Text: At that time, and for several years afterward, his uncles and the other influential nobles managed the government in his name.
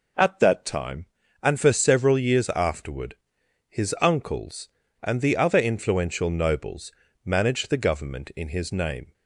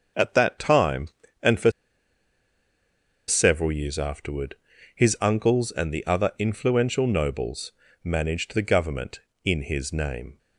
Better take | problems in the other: first | starts louder than the rest; until 1.5 s; 6.5 dB // pauses between "for" and "several"; strong; at 1.6 s; 1.5 s long // pauses between "nobles" and "managed"; slight; at 7.7 s; 0.32 s long; slight in the first

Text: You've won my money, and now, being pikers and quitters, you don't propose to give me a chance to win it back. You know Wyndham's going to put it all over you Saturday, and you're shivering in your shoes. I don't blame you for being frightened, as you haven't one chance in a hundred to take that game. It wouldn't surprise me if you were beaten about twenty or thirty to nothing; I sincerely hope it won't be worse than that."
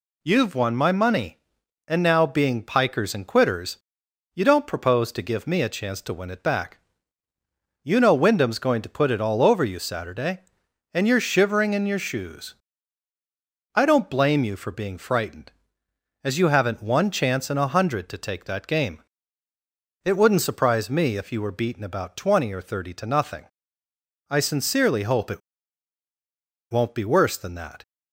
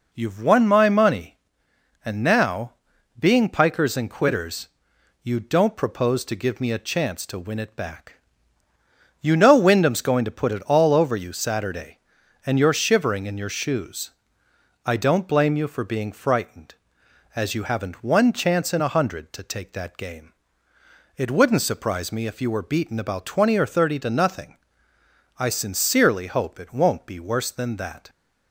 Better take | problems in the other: second | pauses between "it" and "won't"; strong; at 25.4 s; 1.3 s long

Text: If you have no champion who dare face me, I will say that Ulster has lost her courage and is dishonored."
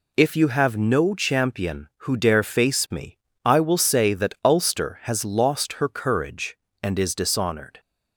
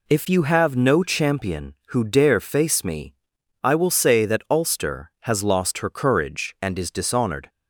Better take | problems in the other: neither | none

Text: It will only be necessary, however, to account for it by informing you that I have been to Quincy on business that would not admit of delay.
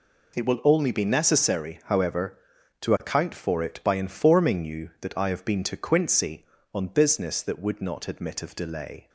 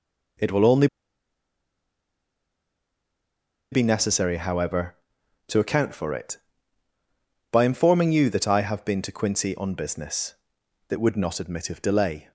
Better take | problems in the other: first | pauses between "only" and "be"; strong; at 0.8 s; 2.8 s long

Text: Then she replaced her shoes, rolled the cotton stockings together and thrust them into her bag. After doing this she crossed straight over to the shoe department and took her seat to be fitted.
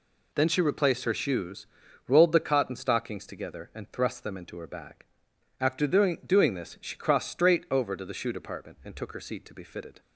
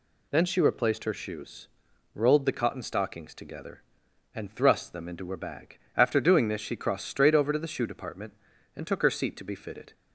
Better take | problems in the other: second | says "doing" twice; at 6.2 s

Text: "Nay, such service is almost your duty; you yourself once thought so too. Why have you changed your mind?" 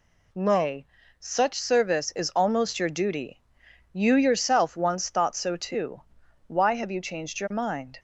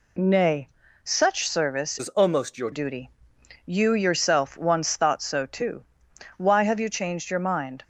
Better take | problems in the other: first | changes voice from "is" to "your"; from 1.9 to 2.7 s; 0.8 s long

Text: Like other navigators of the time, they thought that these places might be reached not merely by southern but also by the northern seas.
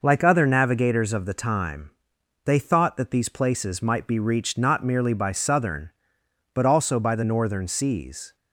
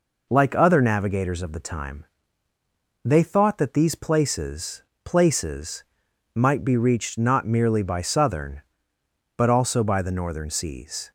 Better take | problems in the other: first | says "places" twice; at 5.0 s

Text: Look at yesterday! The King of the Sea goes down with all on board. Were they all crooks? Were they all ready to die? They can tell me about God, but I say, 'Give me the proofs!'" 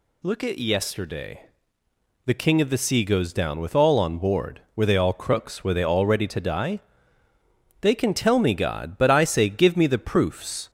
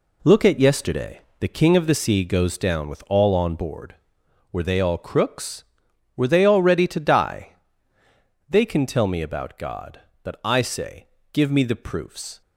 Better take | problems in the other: second | skips "about"; at 8.5 s

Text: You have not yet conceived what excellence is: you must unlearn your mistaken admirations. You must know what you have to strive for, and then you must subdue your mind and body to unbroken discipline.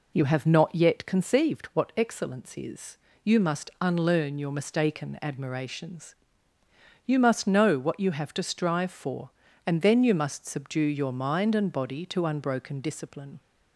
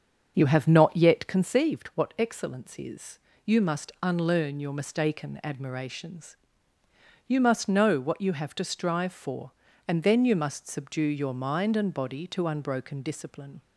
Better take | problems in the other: first | starts louder than the rest; until 1.6 s; 7 dB

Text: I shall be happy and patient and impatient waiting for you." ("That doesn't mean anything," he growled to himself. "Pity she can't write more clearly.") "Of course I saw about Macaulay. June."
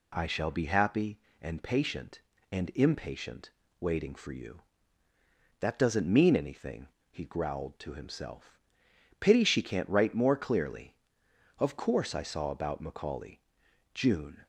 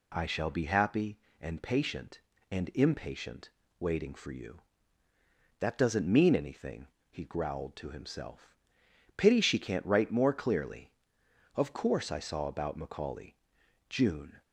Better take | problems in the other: neither | pauses between "impatient" and "waiting"; slight; the same in both

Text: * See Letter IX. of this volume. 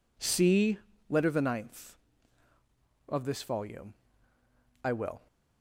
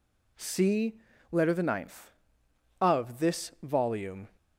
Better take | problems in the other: second | pauses between "See" and "Letter"; slight; at 0.7 s; 0.30 s long; slight in the second // goes on to say "I will"; slight; from 4.8 s on; 0.44 s long

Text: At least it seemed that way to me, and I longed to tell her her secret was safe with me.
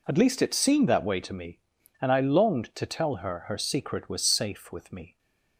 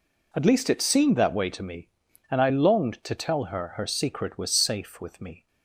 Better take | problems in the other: neither | none

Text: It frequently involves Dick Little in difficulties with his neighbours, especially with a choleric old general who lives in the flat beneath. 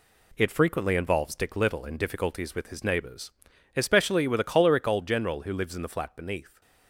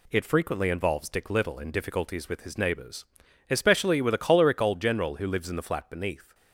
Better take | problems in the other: second | gets quieter; noticeable; throughout; 5.5 dB

